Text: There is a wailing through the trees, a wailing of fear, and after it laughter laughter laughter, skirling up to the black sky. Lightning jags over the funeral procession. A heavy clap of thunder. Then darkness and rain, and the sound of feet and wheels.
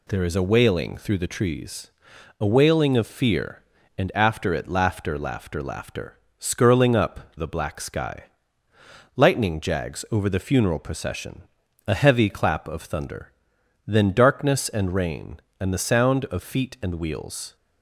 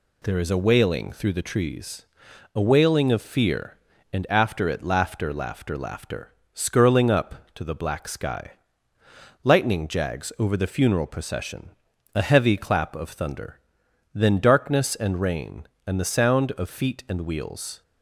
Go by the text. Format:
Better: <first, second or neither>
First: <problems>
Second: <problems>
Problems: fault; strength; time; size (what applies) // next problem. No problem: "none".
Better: second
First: skips "to"; at 7.3 s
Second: none